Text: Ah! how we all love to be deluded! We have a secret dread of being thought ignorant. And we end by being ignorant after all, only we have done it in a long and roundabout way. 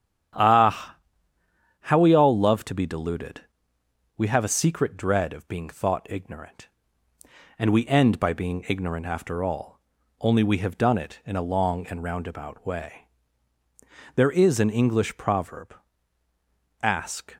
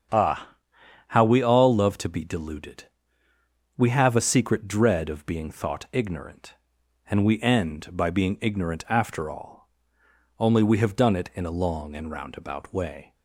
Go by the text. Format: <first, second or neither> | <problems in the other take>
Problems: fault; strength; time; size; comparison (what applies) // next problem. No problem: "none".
second | starts louder than the rest; strong; until 2.2 s; 9.5 dB; strong in the second // goes on to say "There is an English proverb Ask"; strong; from 14.1 s on; 3.2 s long